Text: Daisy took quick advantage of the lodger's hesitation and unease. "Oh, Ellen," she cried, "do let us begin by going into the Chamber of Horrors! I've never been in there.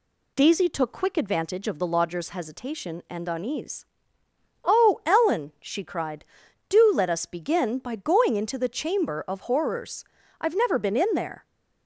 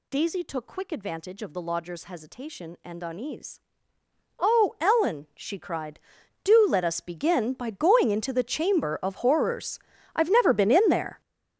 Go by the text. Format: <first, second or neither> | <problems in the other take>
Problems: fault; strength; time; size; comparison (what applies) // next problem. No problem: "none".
first | gets louder; strong; throughout; 14 dB